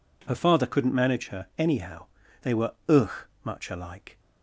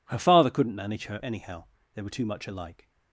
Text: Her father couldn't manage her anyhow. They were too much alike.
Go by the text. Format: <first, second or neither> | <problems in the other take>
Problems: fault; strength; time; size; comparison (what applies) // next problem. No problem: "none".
second | says "ugh" for "too"; at 2.8 s